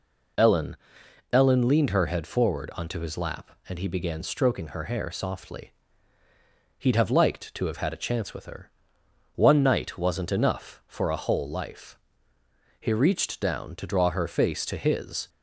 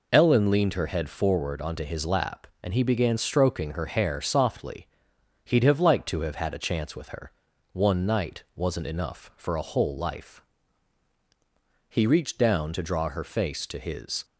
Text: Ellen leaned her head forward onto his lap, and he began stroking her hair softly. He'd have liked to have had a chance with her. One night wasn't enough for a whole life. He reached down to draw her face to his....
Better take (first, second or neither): second